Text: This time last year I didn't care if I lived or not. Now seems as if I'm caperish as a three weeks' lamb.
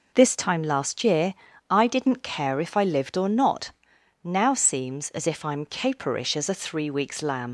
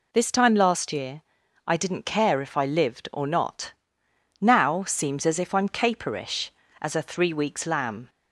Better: second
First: pauses between "year" and "I"; at 1.3 s; 0.38 s long // leaves "lamb" unfinished; at 7.4 s; 90 ms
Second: pauses between "year" and "I"; noticeable; at 1.2 s; 0.46 s long

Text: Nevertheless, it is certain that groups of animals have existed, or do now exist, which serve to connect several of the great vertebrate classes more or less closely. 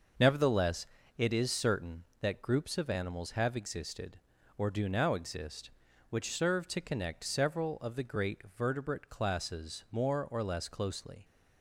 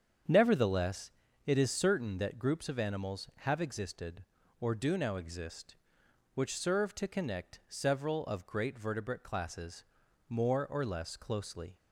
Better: first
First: starts louder than the rest; noticeable; until 1.4 s; 6 dB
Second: starts louder than the rest; strong; until 1.6 s; 8 dB // skips "the"; at 8.4 s // pauses between "classes" and "more"; at 9.8 s; 0.44 s long

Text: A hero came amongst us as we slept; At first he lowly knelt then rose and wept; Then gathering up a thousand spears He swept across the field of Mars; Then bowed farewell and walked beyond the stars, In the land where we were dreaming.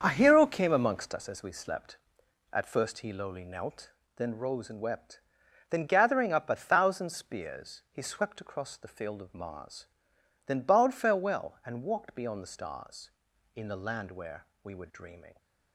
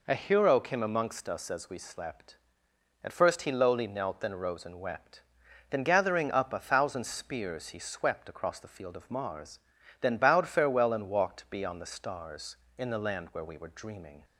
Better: second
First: starts louder than the rest; until 1.3 s; 7 dB // pauses between "knelt" and "then"; slight; at 3.9 s; 0.24 s long // pauses between "where" and "we"; slight; at 14.4 s; 0.18 s long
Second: none

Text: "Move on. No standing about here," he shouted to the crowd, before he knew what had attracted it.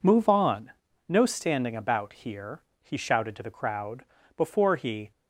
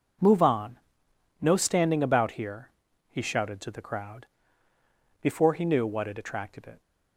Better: second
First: stops before "knew what had attracted it"; at 5.1 s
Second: none

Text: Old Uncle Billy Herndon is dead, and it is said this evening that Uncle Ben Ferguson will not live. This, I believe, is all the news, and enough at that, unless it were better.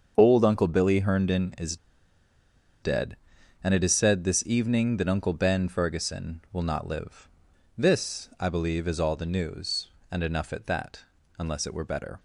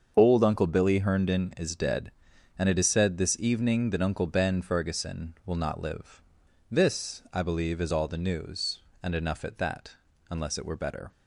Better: second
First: starts louder than the rest; until 1.1 s; 7 dB // pauses between "is" and "dead"; at 1.7 s; 1.0 s long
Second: starts louder than the rest; until 1.1 s; 7 dB

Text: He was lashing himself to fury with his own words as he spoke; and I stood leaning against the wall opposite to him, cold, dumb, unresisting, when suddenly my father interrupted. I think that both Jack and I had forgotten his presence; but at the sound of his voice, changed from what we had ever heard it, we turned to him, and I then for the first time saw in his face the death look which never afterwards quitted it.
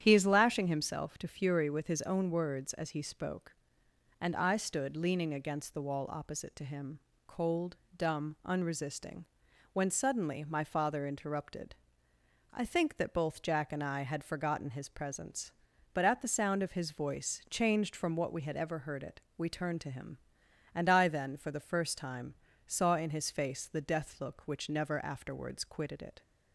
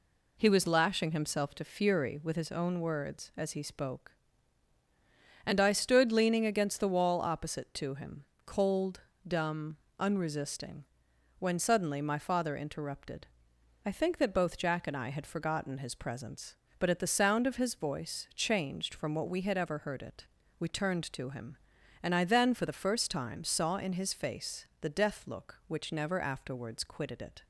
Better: second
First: starts louder than the rest; strong; until 1.0 s; 9.5 dB // says "is" for "was"; at 0.1 s // pauses between "time" and "saw"; slight; at 22.3 s; 0.32 s long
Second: none

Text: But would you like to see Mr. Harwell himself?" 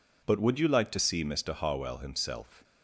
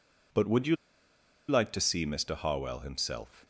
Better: first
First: none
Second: pauses between "you" and "like"; noticeable; at 0.7 s; 0.73 s long

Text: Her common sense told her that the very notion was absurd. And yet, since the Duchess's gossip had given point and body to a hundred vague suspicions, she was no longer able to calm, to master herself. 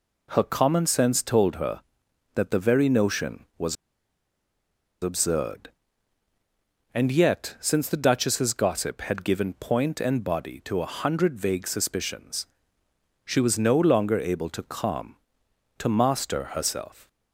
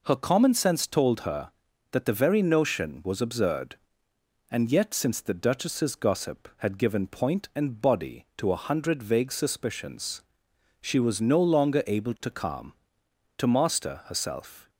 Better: second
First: pauses between "was" and "absurd"; strong; at 3.7 s; 1.2 s long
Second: none

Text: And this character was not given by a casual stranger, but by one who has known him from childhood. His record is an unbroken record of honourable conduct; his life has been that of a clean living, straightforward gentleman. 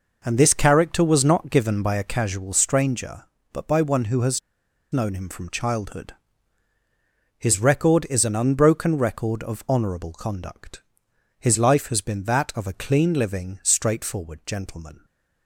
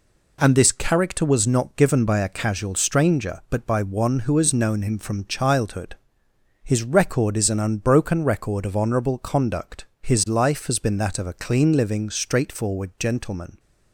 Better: second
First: pauses between "has" and "known"; noticeable; at 4.3 s; 0.52 s long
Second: none

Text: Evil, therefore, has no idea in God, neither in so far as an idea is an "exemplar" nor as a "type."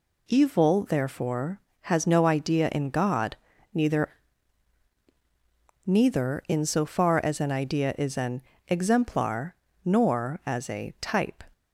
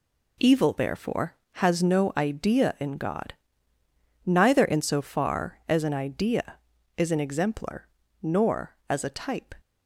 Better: second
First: says "neither" twice; at 5.8 s // pauses between "an" and "exemplar"; slight; at 8.4 s; 0.26 s long // pauses between "exemplar" and "nor"; slight; at 9.5 s; 0.30 s long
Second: pauses between "exemplar" and "nor"; slight; at 7.8 s; 0.34 s long

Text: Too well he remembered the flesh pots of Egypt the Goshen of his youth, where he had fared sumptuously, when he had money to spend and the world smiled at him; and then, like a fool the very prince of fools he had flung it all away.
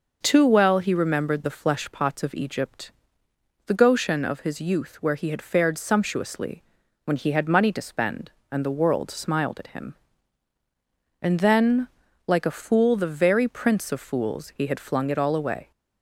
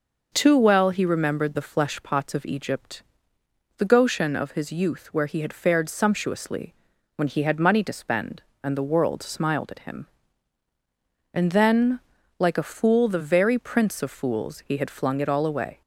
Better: neither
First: pauses between "Egypt" and "the"; noticeable; at 2.9 s; 0.76 s long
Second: pauses between "Egypt" and "the"; noticeable; at 3.0 s; 0.76 s long

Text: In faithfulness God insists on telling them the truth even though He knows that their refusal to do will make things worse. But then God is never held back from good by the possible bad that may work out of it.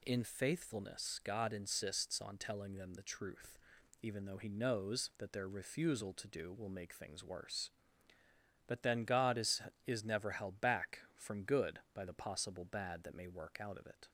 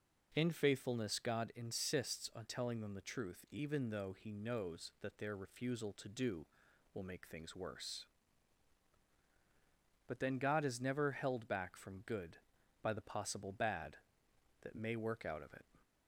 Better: second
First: pauses between "truth" and "even"; noticeable; at 3.5 s; 0.48 s long // says "is" twice; at 9.8 s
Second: none

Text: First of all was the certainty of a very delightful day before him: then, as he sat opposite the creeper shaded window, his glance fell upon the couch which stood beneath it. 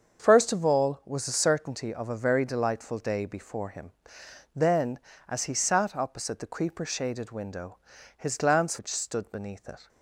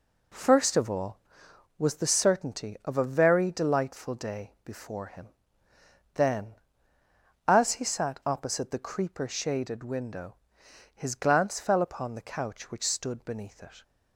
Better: second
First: starts louder than the rest; until 1.3 s; 6.5 dB // skips "fell upon the couch"; at 8.7 s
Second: none

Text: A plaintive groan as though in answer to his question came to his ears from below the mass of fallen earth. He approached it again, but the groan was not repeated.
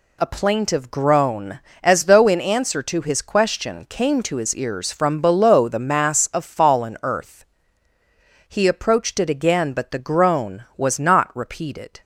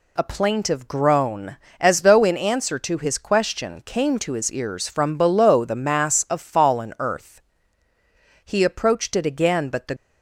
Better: first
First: none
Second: stops before "groan was not repeated"; at 9.9 s

